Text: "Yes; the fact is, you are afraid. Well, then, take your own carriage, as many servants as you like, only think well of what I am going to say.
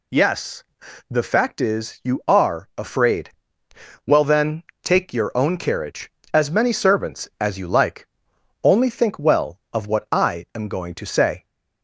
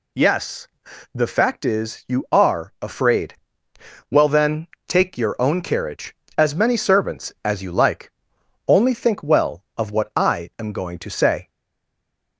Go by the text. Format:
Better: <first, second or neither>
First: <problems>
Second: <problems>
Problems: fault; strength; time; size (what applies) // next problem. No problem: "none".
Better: first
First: none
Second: stays silent after the last word; slight; from 11.4 s on; 0.9 s long